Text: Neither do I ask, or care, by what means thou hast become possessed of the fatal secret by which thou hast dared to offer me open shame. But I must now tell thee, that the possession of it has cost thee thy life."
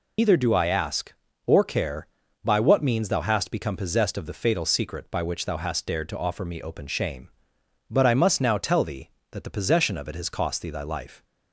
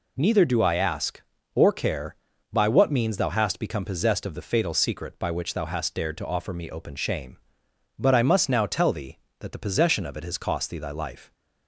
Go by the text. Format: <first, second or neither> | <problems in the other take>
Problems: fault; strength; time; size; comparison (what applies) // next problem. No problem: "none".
second | loses the start of "Neither"; at 0.1 s; 100 ms